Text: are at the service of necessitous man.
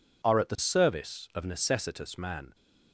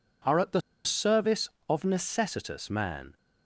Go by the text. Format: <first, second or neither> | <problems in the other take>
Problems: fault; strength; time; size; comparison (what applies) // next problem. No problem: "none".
first | pauses between "the" and "service"; slight; at 0.6 s; 0.24 s long